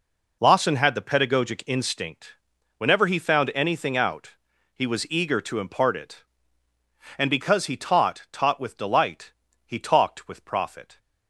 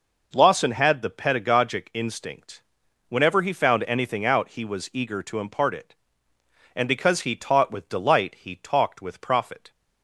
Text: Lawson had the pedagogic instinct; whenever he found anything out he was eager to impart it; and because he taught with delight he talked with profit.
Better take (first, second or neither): second